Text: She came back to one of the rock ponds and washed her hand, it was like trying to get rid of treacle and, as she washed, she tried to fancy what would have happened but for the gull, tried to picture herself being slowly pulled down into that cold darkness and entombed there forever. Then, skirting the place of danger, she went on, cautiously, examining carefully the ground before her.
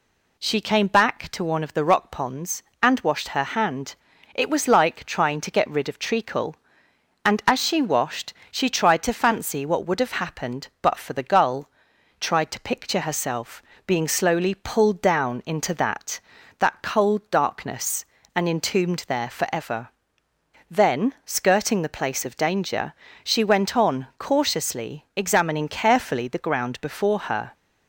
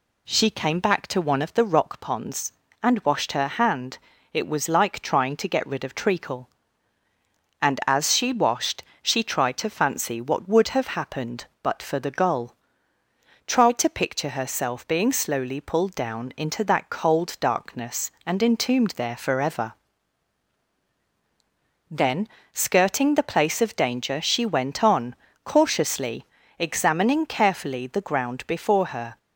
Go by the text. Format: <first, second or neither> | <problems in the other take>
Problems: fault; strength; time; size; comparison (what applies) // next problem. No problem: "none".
second | pauses between "herself" and "being"; slight; at 13.6 s; 0.24 s long // says "that" twice; at 16.5 s